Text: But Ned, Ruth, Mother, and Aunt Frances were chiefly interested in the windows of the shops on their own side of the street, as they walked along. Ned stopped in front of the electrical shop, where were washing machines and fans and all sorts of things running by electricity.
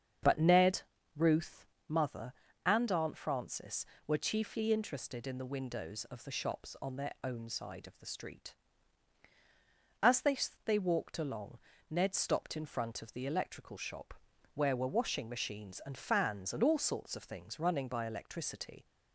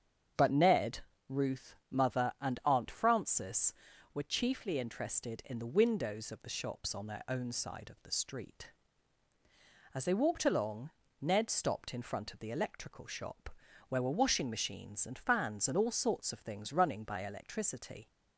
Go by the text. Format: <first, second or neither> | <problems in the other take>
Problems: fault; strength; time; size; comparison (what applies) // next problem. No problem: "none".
second | starts louder than the rest; strong; until 1.5 s; 7 dB; strong in the second // says "they" twice; at 10.6 s